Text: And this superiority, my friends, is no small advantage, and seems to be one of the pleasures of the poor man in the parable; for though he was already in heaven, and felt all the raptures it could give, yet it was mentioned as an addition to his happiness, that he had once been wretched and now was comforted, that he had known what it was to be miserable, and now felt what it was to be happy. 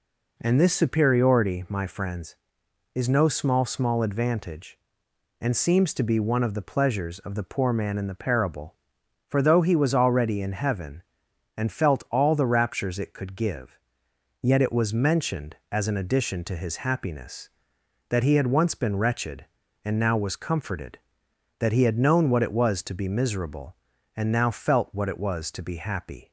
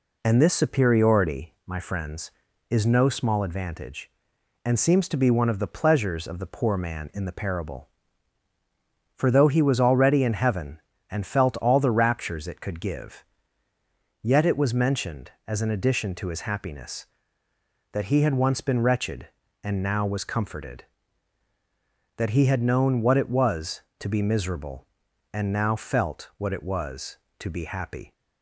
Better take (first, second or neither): second